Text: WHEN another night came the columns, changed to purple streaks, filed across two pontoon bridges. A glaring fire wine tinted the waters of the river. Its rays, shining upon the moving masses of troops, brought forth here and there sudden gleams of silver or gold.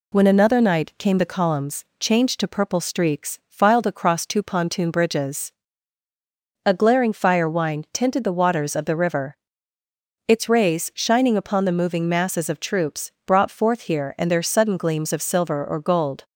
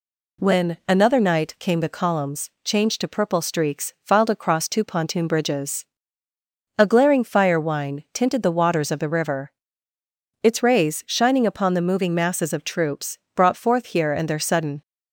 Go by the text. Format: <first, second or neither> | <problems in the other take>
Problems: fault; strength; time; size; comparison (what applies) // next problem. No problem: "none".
first | stops before "gleams of silver or gold"; at 14.8 s